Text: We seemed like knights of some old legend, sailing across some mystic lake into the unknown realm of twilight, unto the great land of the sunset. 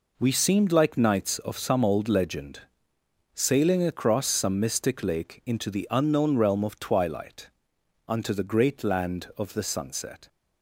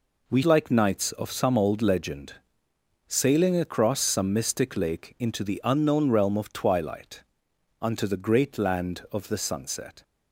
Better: first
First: none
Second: skips "seemed"; at 0.4 s

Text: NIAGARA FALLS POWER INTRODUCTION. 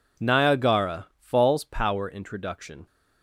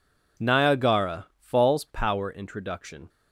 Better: neither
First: none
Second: none

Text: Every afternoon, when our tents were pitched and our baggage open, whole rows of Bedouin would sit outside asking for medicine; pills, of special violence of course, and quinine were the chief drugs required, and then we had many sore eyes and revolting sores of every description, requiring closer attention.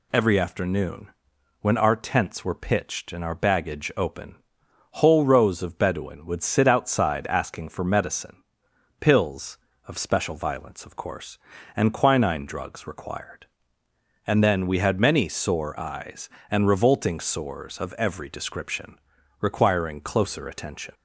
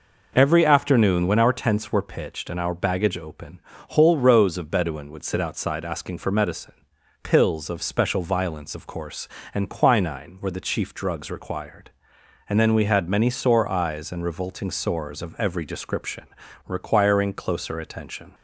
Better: second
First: skips "were the chief"; at 12.4 s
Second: none

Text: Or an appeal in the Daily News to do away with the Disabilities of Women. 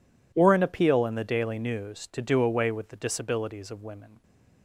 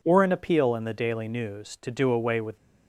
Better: first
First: none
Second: stops before "the Disabilities of Women"; at 2.5 s

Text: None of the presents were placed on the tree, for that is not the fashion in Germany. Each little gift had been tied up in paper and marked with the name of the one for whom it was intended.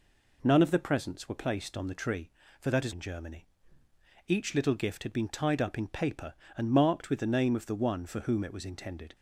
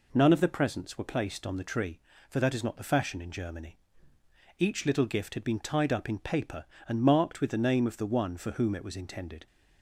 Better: second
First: skips "not the fashion"; at 2.9 s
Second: none

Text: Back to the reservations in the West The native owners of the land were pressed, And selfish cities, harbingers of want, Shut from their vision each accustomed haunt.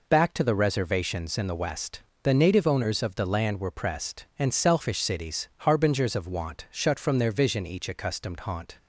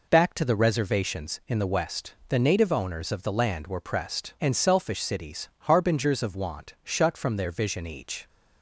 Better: first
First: pauses between "West" and "The"; slight; at 2.0 s; 0.22 s long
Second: pauses between "West" and "The"; slight; at 2.1 s; 0.16 s long // stops before "accustomed haunt"; at 8.2 s

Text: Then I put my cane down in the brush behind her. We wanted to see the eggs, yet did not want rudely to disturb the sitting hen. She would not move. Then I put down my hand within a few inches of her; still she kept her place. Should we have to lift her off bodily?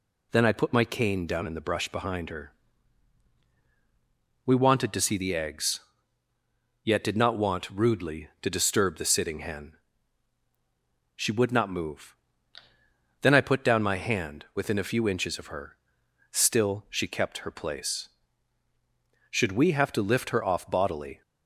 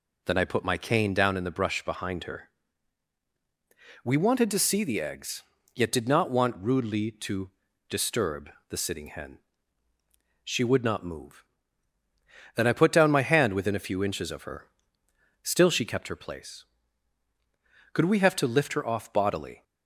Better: first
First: none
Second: pauses between "to" and "disturb"; at 7.4 s; 0.40 s long // pauses between "disturb" and "the"; slight; at 8.4 s; 0.20 s long // says "Could" for "Should"; at 17.9 s

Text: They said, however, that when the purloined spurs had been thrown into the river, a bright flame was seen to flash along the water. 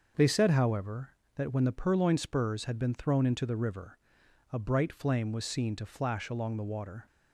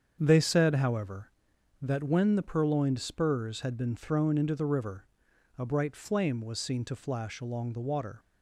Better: neither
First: starts louder than the rest; until 1.4 s; 6.5 dB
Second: starts louder than the rest; strong; until 1.2 s; 7.5 dB

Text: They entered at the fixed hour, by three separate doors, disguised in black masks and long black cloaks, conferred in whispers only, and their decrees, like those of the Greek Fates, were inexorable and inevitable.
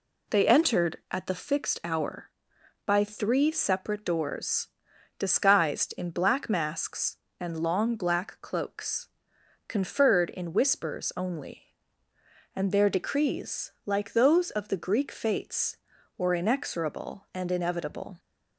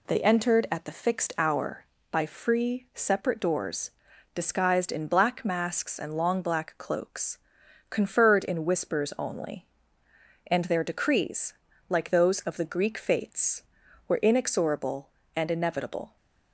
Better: first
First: none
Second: says "free" for "three"; at 2.2 s

